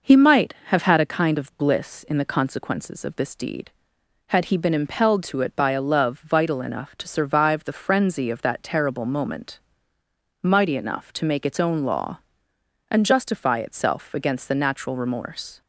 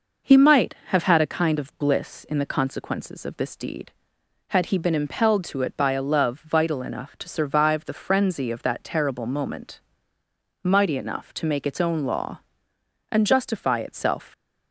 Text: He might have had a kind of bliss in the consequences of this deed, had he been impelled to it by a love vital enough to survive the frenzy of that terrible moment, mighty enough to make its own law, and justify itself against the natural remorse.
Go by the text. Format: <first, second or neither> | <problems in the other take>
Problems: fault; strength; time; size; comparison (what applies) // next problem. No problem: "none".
first | stops before "against the natural remorse"; at 14.3 s